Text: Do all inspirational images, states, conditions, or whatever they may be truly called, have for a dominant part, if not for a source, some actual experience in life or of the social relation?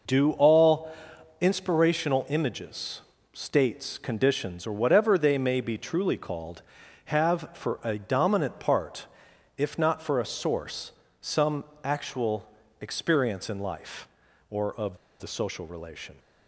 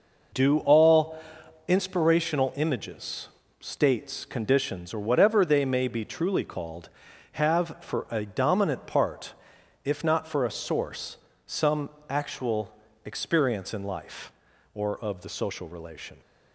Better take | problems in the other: second | pauses between "all" and "inspirational"; noticeable; at 0.9 s; 0.48 s long; noticeable in the second // pauses between "some" and "actual"; slight; at 11.6 s; 0.18 s long; slight in the second // pauses between "actual" and "experience"; slight; at 12.4 s; 0.32 s long; slight in the second // pauses between "of" and "the"; slight; at 14.9 s; 0.23 s long

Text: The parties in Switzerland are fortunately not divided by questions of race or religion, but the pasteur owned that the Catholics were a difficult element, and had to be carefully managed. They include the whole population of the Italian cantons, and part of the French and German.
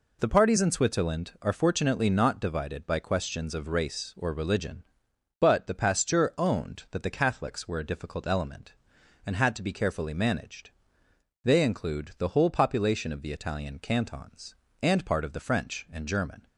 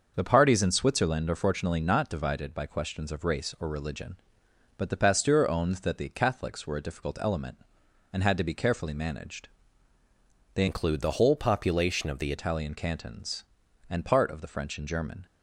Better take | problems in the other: first | starts louder than the rest; until 1.1 s; 6.5 dB // changes voice from "include" to "the"; from 10.6 to 12.3 s; 1.7 s long

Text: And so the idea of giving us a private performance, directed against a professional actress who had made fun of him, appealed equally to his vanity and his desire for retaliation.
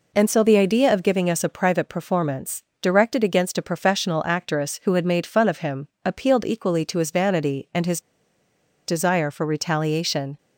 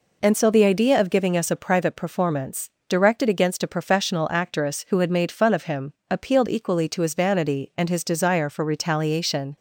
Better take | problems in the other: second | pauses between "his" and "desire"; noticeable; at 8.0 s; 0.86 s long

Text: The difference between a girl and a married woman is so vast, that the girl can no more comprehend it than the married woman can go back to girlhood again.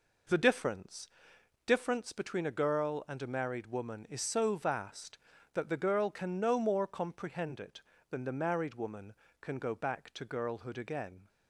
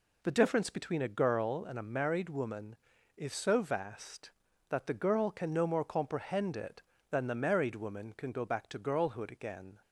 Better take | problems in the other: second | says "difference" twice; at 1.6 s

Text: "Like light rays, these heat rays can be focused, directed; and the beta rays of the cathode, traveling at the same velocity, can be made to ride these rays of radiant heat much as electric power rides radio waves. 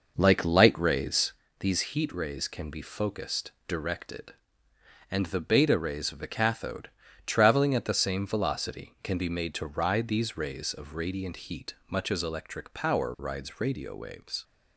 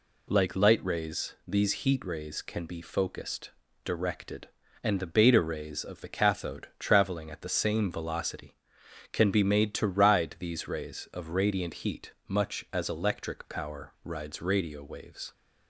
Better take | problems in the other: second | starts louder than the rest; noticeable; until 1.5 s; 5.5 dB

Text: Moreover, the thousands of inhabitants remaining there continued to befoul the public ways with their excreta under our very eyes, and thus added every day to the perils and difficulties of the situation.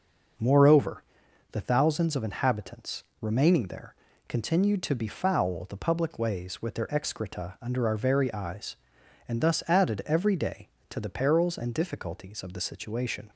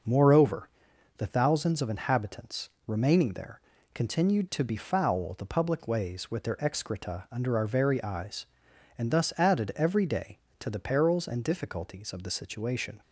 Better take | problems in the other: neither | pauses between "inhabitants" and "remaining"; slight; the same in both // pauses between "there" and "continued"; slight; the same in both

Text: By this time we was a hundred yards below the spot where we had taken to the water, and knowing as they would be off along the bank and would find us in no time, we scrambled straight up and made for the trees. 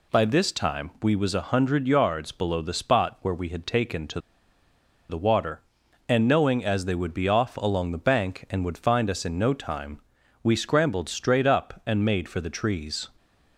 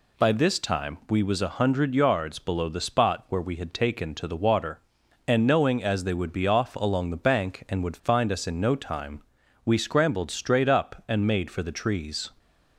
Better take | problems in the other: second | pauses between "to" and "the"; noticeable; at 4.1 s; 0.90 s long

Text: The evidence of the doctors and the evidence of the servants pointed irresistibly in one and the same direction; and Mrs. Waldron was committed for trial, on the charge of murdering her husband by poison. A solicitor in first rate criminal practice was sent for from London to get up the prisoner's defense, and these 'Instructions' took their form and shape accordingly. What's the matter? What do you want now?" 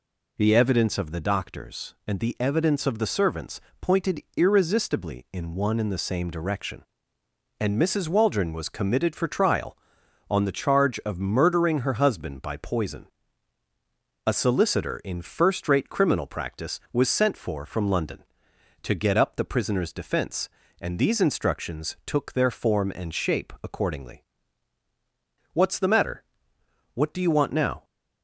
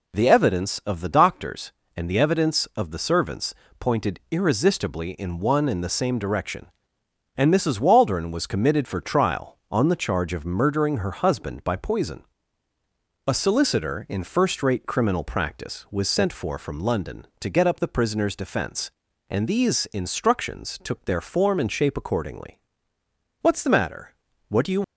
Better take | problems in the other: first | pauses between "servants" and "pointed"; slight; at 3.5 s; 0.24 s long; slight in the first // stops before "want now"; at 24.8 s

